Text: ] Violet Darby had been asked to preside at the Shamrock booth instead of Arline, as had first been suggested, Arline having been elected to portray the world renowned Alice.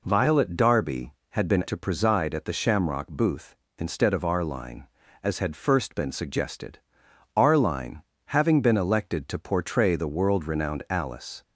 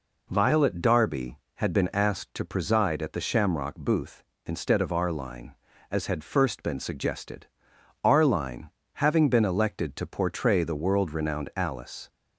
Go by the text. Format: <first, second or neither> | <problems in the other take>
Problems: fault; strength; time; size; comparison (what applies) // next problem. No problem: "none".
second | skips "asked"; at 1.6 s // pauses between "Arline" and "having"; slight; at 8.0 s; 0.24 s long; slight in the second